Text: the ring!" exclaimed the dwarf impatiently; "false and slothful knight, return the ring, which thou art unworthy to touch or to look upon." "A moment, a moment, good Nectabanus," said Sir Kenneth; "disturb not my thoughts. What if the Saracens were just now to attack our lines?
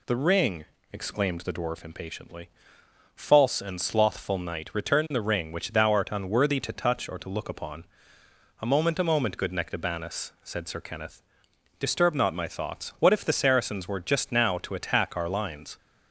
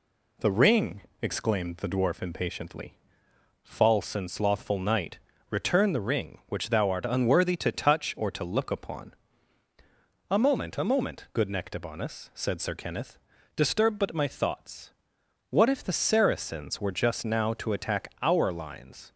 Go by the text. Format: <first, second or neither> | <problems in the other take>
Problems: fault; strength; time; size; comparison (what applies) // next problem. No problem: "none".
first | says "but" for "not"; at 13.9 s